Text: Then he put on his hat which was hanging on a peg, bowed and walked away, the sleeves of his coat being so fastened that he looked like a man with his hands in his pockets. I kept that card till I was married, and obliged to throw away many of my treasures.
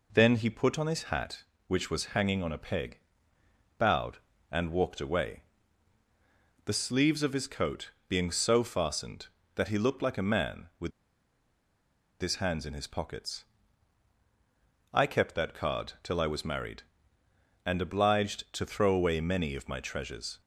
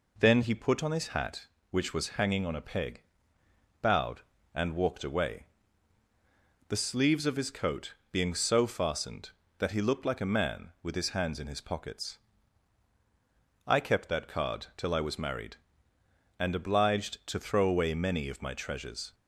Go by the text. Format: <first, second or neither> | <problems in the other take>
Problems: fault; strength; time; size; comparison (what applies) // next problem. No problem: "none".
second | pauses between "coat" and "being"; slight; at 7.9 s; 0.18 s long; slight in the second // pauses between "with" and "his"; strong; at 10.9 s; 1.2 s long